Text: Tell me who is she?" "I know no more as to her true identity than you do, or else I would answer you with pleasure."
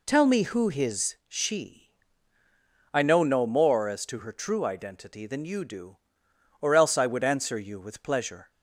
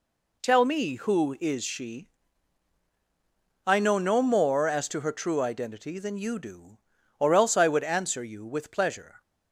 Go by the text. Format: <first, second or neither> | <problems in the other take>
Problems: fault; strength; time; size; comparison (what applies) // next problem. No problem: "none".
second | says "his" for "is"; at 0.6 s